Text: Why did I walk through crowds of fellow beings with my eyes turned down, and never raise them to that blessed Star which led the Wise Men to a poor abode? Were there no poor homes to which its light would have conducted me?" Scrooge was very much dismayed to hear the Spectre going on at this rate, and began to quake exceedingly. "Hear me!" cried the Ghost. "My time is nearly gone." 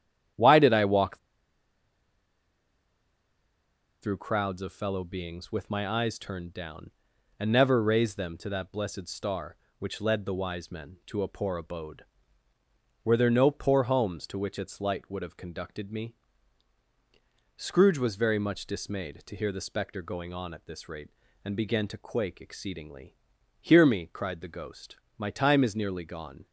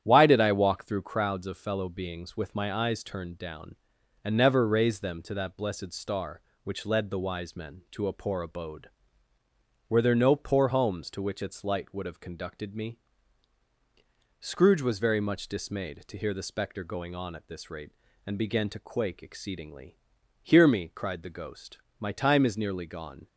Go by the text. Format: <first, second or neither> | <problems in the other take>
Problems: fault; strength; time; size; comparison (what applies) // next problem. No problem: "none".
second | starts louder than the rest; strong; until 4.2 s; 10 dB; strong in the second // pauses between "walk" and "through"; strong; at 1.1 s; 2.8 s long